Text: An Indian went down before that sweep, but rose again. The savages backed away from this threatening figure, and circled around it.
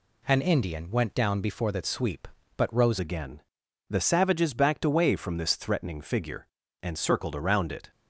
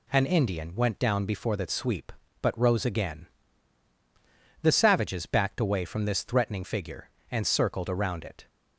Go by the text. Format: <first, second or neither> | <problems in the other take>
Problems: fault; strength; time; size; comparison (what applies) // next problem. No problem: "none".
second | changes voice at "again"; from 2.9 s on; 5.0 s long